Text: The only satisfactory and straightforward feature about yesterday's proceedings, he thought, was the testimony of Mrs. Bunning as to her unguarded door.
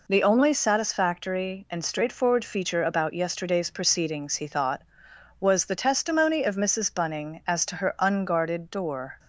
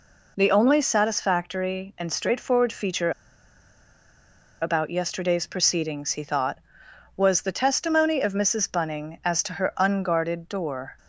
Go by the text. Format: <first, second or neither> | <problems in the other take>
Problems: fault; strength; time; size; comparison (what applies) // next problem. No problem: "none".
first | pauses between "feature" and "about"; strong; at 3.1 s; 1.5 s long